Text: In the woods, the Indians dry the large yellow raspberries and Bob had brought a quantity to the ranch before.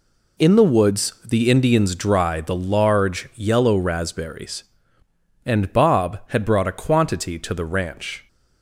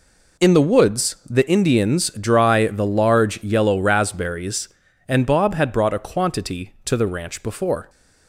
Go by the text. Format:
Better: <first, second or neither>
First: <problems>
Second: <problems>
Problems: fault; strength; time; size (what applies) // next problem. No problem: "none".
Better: second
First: stops before "before"; at 8.2 s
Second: none